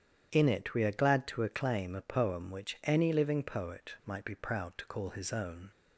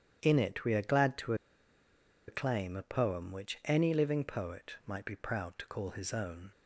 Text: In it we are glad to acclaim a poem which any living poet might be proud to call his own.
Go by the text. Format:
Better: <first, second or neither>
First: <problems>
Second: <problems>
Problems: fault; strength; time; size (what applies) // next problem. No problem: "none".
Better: first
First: starts louder than the rest; strong; until 1.3 s; 9.5 dB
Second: starts louder than the rest; strong; until 1.2 s; 9.5 dB // pauses between "to" and "acclaim"; noticeable; at 1.3 s; 0.93 s long